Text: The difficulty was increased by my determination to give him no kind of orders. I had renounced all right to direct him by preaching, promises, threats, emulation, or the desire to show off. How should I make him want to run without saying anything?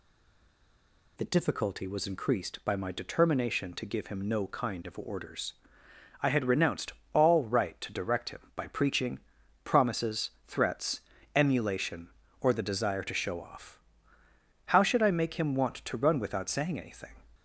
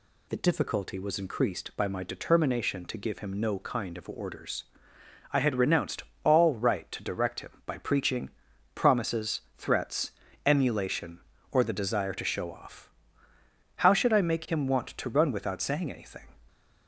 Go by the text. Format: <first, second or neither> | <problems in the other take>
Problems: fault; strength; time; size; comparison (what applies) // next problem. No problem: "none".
second | stays silent before the first word; noticeable; until 1.1 s; 1.1 s long // pauses between "renounced" and "all"; slight; at 6.9 s; 0.20 s long; slight in the second